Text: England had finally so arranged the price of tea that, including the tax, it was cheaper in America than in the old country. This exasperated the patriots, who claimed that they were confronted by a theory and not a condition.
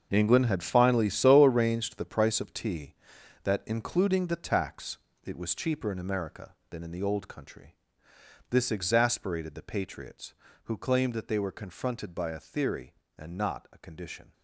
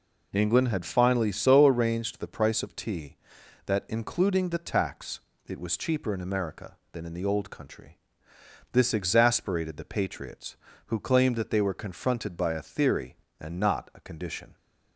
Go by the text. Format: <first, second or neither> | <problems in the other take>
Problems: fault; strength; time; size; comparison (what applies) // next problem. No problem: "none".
second | gets quieter; strong; throughout; 13 dB